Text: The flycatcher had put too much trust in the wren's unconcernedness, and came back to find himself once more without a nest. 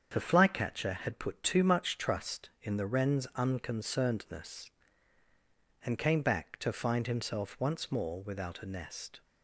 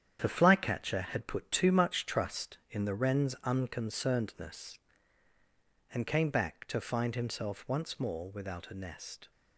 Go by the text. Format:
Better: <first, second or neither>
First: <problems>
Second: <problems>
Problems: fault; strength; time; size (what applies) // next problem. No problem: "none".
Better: first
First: starts louder than the rest; strong; until 1.1 s; 7.5 dB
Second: gets quieter; strong; throughout; 8 dB // starts louder than the rest; strong; until 1.2 s; 9 dB